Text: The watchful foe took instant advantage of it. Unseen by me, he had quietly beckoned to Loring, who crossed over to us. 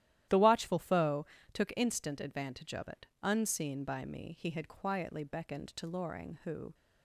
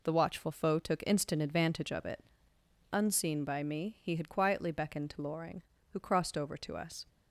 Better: second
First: starts louder than the rest; strong; until 1.6 s; 12.5 dB // pauses between "foe" and "took"; slight; at 1.2 s; 0.30 s long // stops before "crossed over to us"; at 6.7 s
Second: none

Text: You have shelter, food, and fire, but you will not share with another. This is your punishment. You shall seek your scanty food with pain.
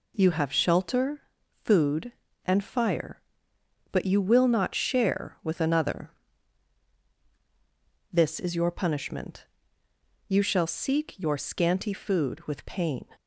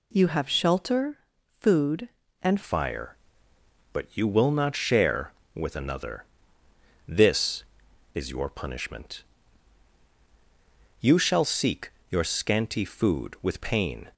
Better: first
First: none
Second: changes voice at "fire"; from 2.6 s on; 11.5 s long // pauses between "seek" and "your"; slight; at 11.9 s; 0.20 s long

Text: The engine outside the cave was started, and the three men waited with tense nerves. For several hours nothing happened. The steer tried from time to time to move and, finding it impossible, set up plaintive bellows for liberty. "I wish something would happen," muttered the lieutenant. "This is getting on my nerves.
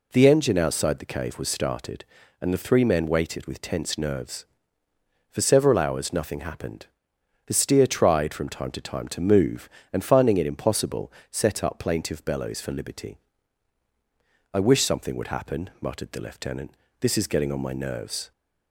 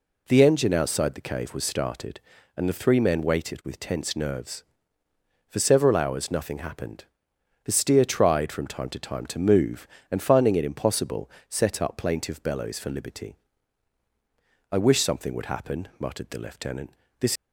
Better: first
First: none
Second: stops before "is getting on my nerves"; at 17.3 s

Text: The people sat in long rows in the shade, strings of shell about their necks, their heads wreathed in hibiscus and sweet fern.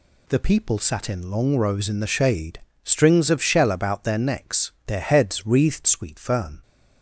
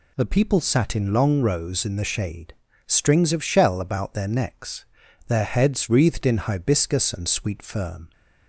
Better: second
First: skips "in hibiscus and"; at 5.8 s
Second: none

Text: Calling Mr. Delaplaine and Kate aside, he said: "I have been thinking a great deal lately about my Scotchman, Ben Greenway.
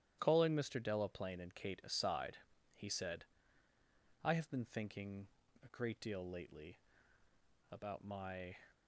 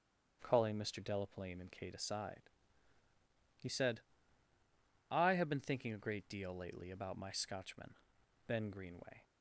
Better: second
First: starts louder than the rest; strong; until 1.2 s; 11 dB // pauses between "thinking" and "a"; slight; at 5.2 s; 0.34 s long // pauses between "lately" and "about"; noticeable; at 6.7 s; 0.90 s long // stops before "Scotchman Ben Greenway"; at 8.7 s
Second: starts louder than the rest; strong; until 1.4 s; 8 dB

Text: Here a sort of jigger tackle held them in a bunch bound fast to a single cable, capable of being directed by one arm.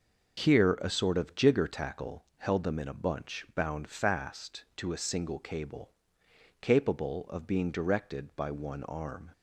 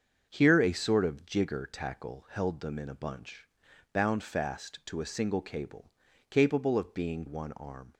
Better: first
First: starts louder than the rest; until 1.5 s; 7 dB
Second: starts louder than the rest; until 1.3 s; 6.5 dB // pauses between "bunch" and "bound"; noticeable; at 3.4 s; 0.48 s long // skips "directed by"; at 7.2 s

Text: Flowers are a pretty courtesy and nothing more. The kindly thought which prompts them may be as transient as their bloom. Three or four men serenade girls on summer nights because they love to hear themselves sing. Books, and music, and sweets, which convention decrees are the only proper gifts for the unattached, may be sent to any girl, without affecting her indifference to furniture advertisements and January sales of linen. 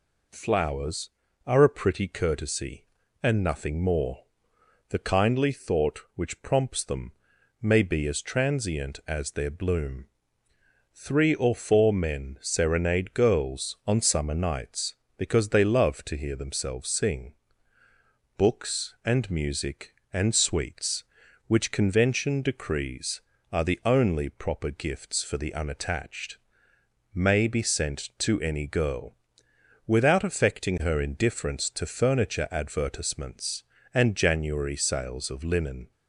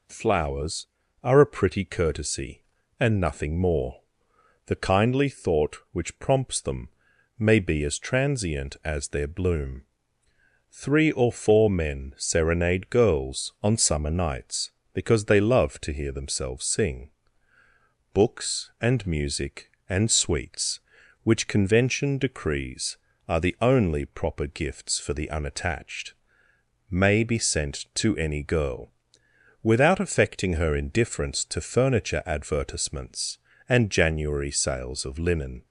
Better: neither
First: pauses between "them" and "may"; noticeable; at 7.1 s; 0.50 s long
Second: pauses between "them" and "may"; noticeable; at 6.8 s; 0.50 s long

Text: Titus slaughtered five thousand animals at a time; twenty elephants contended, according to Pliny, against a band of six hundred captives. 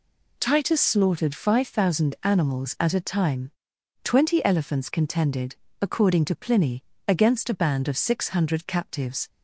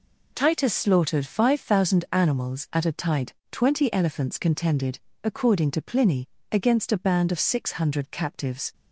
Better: first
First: none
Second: says "tide" for "time"; at 2.9 s

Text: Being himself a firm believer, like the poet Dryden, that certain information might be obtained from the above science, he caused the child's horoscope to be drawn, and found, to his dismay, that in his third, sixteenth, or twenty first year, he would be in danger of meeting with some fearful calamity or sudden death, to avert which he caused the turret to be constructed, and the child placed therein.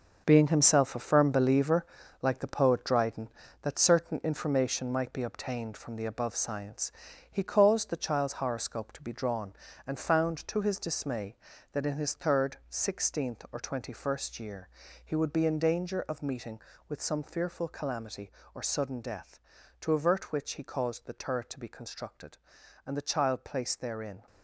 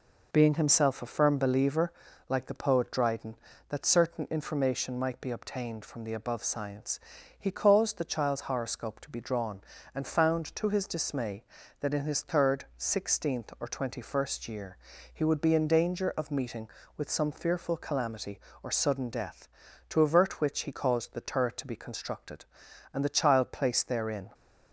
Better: second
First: gets quieter; strong; throughout; 9.5 dB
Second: none

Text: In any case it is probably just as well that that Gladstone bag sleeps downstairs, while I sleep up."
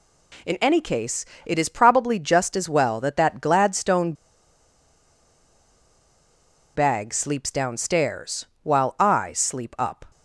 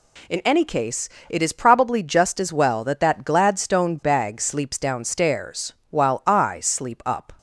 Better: second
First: pauses between "case" and "it"; slight; at 1.2 s; 0.20 s long // pauses between "Gladstone" and "bag"; strong; at 4.1 s; 2.6 s long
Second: pauses between "case" and "it"; slight; at 1.0 s; 0.20 s long

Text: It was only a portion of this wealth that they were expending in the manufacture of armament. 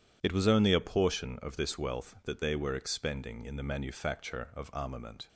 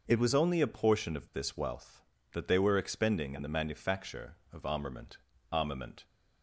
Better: first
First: none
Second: says "armament" twice; at 5.5 s

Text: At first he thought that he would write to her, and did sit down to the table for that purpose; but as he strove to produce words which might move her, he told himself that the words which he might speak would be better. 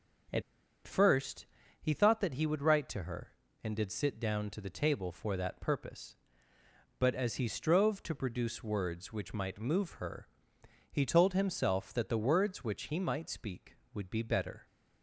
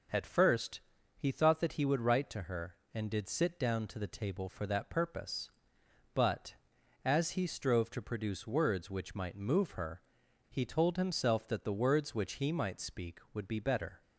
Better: second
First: starts louder than the rest; until 2.1 s; 7 dB // pauses between "At" and "first"; at 0.4 s; 0.45 s long // pauses between "first" and "he"; slight; at 1.4 s; 0.34 s long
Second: pauses between "first" and "he"; slight; at 0.7 s; 0.36 s long

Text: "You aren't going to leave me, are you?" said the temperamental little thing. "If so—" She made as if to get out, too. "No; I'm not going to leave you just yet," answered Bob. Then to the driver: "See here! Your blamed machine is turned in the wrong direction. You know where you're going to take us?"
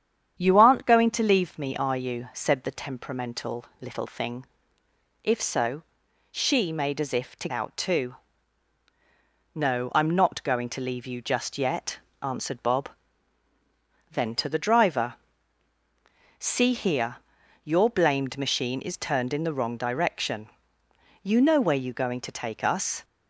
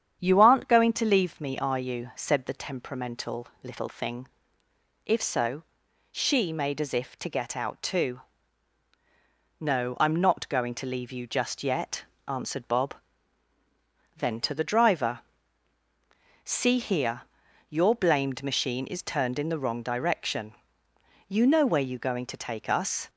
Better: second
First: starts louder than the rest; strong; until 1.4 s; 8.5 dB // pauses between "temperamental" and "little"; slight; at 3.6 s; 0.16 s long // skips "get"; at 7.4 s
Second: starts louder than the rest; strong; until 1.2 s; 8.5 dB // pauses between "temperamental" and "little"; slight; at 3.4 s; 0.16 s long

